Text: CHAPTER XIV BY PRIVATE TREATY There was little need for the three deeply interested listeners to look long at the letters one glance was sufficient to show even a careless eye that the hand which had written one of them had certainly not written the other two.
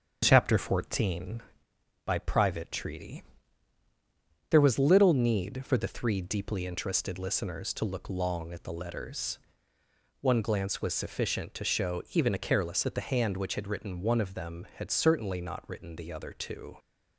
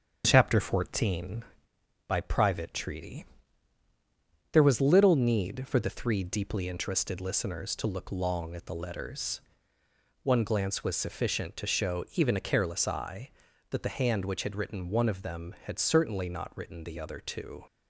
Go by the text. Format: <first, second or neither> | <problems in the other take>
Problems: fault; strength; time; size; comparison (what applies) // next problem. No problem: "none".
second | starts louder than the rest; strong; until 1.2 s; 8 dB; strong in the second // pauses between "TREATY" and "There"; strong; at 3.2 s; 1.2 s long; strong in the second // pauses between "letters" and "one"; noticeable; at 9.3 s; 0.84 s long; noticeable in the second // skips "eye"; at 12.8 s